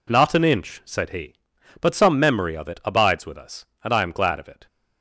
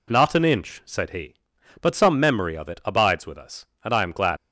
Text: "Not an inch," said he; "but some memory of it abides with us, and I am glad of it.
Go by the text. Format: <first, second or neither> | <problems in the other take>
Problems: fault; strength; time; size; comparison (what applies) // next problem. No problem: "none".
first | stops before "of it"; at 4.3 s